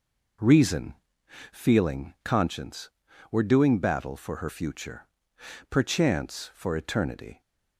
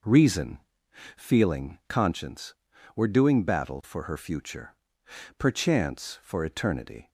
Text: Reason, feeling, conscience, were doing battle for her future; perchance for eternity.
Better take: neither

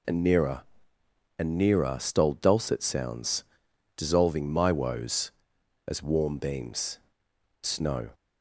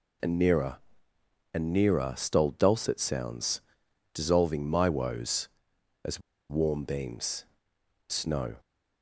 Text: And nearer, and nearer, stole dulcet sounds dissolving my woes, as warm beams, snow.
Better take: first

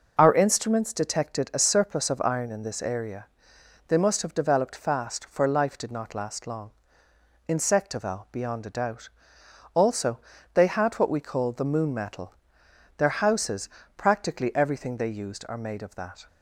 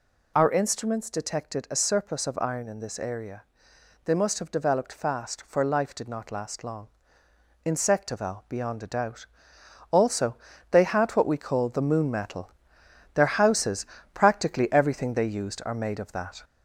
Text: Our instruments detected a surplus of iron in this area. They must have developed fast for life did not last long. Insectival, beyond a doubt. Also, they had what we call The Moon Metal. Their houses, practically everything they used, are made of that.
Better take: first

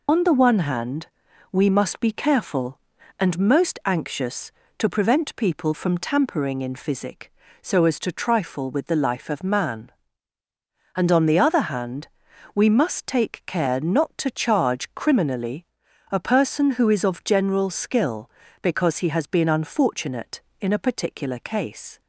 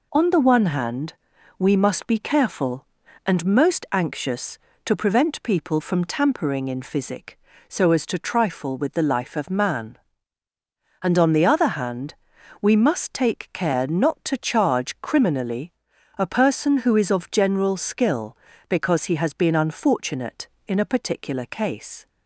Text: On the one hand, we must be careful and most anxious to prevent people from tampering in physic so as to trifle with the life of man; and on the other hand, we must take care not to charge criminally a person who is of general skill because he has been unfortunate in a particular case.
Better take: second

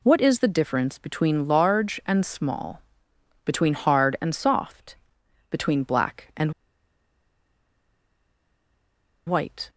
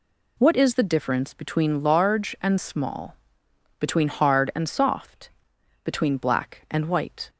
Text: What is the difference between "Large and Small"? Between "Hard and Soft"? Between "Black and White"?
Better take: second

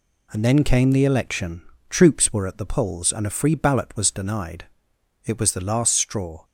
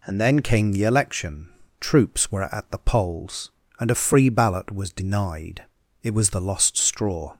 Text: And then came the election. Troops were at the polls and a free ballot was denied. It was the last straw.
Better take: first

